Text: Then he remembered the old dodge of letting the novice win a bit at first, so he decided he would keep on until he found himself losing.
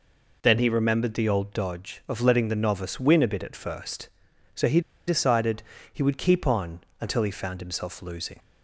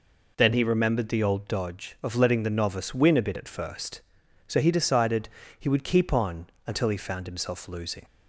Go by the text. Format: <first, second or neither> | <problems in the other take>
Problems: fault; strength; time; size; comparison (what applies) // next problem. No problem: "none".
second | pauses between "he" and "decided"; slight; at 4.7 s; 0.27 s long // pauses between "decided" and "he"; slight; at 5.6 s; 0.30 s long; slight in the second // pauses between "on" and "until"; slight; at 6.8 s; 0.20 s long; slight in the second